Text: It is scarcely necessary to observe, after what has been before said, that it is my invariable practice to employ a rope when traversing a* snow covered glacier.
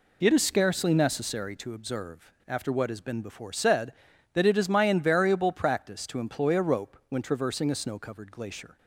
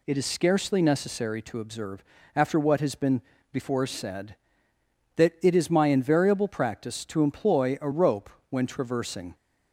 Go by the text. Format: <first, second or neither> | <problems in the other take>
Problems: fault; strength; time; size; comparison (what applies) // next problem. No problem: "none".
first | pauses between "been" and "before"; slight; at 3.2 s; 0.30 s long // pauses between "rope" and "when"; slight; at 8.2 s; 0.20 s long // stops before "a snow covered glacier"; at 9.3 s